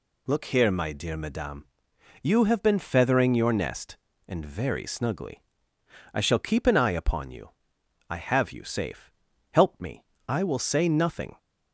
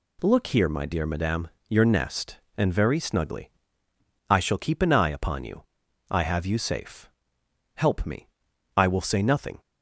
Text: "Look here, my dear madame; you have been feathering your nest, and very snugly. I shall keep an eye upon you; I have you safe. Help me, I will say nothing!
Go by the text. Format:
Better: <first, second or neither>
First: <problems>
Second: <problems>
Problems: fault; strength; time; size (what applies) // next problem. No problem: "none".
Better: first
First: none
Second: skips "you have been feathering"; at 1.5 s